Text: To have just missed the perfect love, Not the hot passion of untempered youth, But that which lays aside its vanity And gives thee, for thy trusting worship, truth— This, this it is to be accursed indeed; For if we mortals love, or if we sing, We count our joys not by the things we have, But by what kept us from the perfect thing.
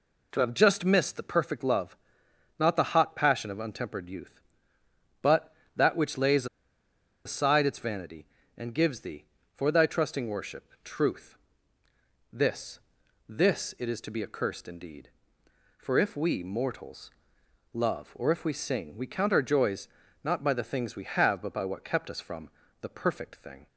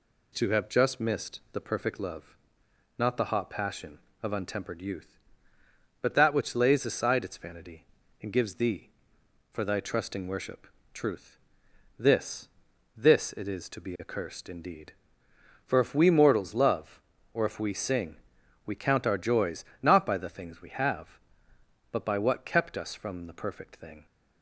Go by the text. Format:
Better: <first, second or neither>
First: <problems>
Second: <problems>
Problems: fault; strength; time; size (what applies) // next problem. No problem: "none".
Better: second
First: pauses between "lays" and "aside"; noticeable; at 6.4 s; 0.79 s long // pauses between "mortals" and "love"; noticeable; at 17.1 s; 0.62 s long // pauses between "joys" and "not"; at 19.8 s; 0.38 s long // pauses between "from" and "the"; slight; at 22.4 s; 0.32 s long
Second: pauses between "joys" and "not"; slight; at 19.6 s; 0.16 s long